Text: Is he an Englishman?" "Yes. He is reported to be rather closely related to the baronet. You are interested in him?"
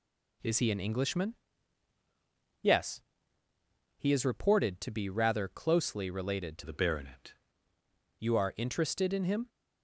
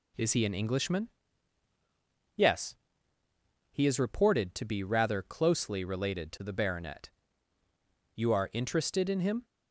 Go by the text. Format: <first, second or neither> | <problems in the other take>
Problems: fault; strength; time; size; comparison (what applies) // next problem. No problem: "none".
second | changes voice from "the" to "baronet"; from 6.6 to 7.3 s; 0.7 s long